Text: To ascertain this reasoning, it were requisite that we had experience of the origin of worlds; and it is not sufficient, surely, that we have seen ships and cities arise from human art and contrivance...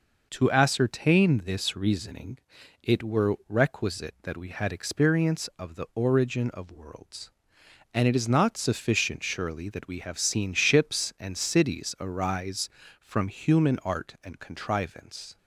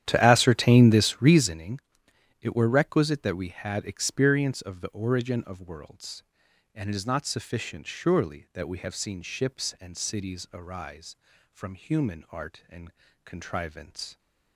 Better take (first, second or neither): first